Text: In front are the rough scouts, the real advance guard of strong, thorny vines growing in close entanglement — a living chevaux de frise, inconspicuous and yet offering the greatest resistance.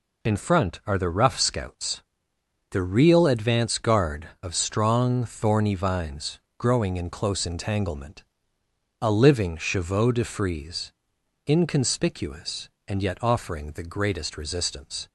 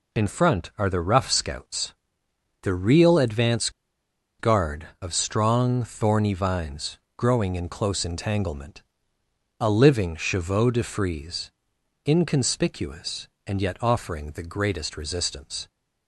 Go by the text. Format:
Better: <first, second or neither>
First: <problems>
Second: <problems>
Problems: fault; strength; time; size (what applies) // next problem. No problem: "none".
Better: first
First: pauses between "vines" and "growing"; slight; at 6.3 s; 0.20 s long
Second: pauses between "advance" and "guard"; noticeable; at 3.6 s; 0.69 s long // pauses between "vines" and "growing"; slight; at 6.9 s; 0.20 s long